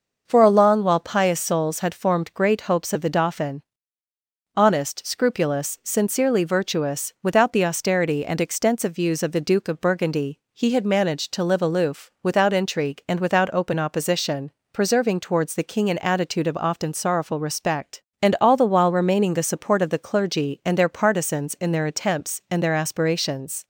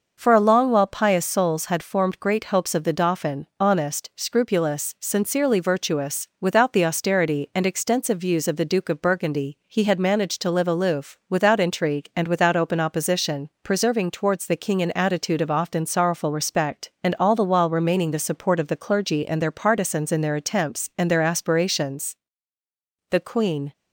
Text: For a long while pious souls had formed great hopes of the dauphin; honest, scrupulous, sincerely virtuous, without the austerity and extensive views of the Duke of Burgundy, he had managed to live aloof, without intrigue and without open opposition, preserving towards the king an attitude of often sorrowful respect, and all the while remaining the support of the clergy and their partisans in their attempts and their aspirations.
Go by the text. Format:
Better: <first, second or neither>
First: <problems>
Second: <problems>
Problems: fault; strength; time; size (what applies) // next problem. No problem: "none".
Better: first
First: starts louder than the rest; until 1.2 s; 6 dB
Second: starts louder than the rest; noticeable; until 1.1 s; 6 dB // goes on to say "The Queen"; noticeable; from 23.1 s on; 0.62 s long